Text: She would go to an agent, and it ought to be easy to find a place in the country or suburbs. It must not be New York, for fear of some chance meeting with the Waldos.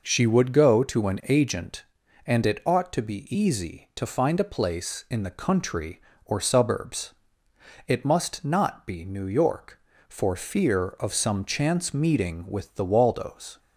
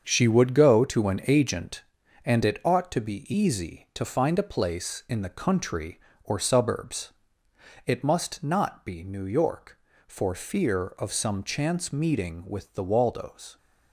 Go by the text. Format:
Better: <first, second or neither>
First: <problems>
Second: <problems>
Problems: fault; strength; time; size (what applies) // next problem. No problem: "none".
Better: first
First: none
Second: gets quieter; strong; throughout; 8 dB